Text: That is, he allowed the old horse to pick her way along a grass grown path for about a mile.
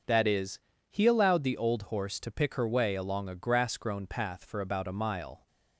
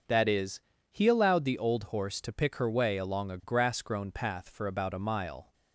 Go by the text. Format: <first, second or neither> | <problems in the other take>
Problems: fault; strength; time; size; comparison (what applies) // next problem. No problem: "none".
neither | starts louder than the rest; the same in both